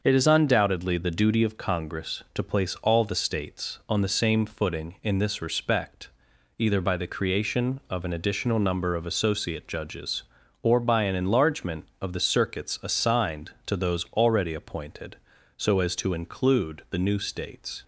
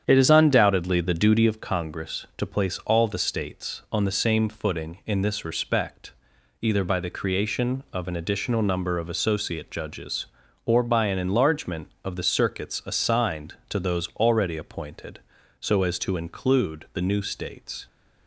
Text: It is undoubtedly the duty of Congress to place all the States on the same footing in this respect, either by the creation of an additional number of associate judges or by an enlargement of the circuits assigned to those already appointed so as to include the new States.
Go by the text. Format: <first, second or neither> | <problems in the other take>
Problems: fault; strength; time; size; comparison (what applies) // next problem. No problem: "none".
first | starts louder than the rest; strong; until 1.6 s; 8 dB